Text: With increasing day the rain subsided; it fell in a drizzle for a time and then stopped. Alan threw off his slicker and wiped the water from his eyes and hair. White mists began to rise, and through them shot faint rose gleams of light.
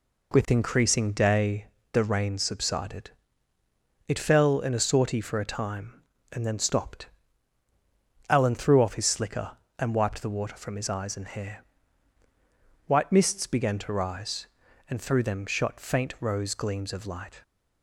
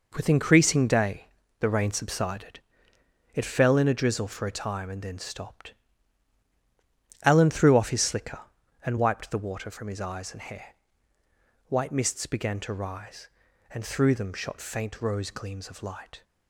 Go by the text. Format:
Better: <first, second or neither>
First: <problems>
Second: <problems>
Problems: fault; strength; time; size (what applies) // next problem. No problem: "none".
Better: second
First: pauses between "day" and "the"; slight; at 1.6 s; 0.26 s long // says "sortie" for "drizzle"; at 4.8 s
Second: pauses between "day" and "the"; slight; at 1.2 s; 0.34 s long